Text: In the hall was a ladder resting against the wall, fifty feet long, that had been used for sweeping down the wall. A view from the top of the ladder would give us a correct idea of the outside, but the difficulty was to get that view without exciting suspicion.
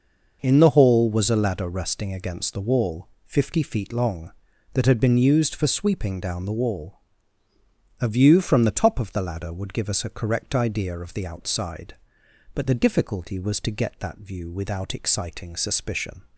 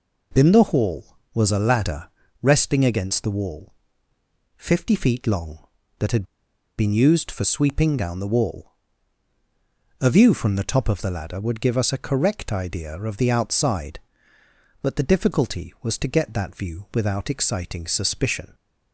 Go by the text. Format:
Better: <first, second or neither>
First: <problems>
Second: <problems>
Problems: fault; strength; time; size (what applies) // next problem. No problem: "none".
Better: first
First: none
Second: pauses between "ladder" and "resting"; slight; at 2.0 s; 0.32 s long // pauses between "had" and "been"; noticeable; at 6.2 s; 0.53 s long